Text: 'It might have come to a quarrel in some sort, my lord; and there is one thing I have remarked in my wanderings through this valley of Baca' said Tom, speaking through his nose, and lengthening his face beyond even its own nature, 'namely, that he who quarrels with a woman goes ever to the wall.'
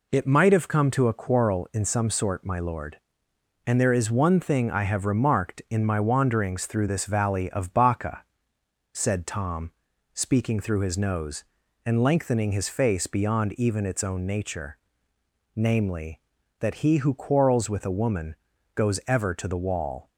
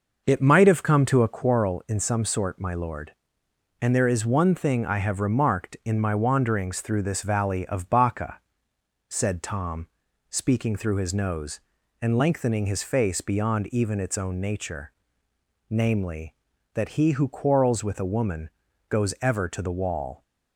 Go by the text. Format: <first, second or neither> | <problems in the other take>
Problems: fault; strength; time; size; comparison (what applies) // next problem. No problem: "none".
first | starts louder than the rest; noticeable; until 1.5 s; 6 dB // pauses between "Baca" and "said"; noticeable; at 8.3 s; 0.70 s long; noticeable in the first // pauses between "woman" and "goes"; at 18.5 s; 0.38 s long; also in the first